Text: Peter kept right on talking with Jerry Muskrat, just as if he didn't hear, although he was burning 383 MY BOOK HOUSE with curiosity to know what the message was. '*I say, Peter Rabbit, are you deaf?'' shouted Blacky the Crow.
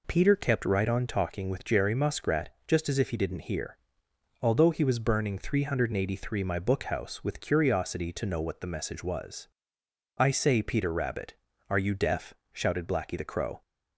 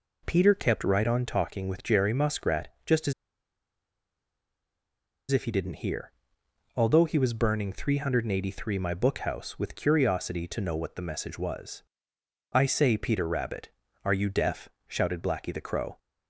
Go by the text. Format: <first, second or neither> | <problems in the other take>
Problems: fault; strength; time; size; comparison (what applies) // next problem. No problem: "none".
first | pauses between "as" and "if"; strong; at 3.1 s; 2.1 s long